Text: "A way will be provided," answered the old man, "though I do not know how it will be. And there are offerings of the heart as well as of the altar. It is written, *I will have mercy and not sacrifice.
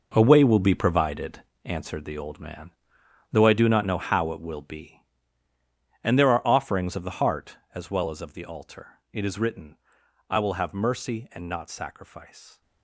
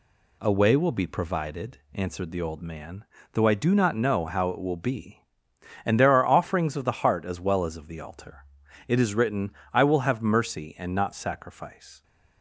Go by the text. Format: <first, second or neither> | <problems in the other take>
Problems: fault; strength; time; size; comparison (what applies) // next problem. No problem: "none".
second | gets quieter; strong; throughout; 12.5 dB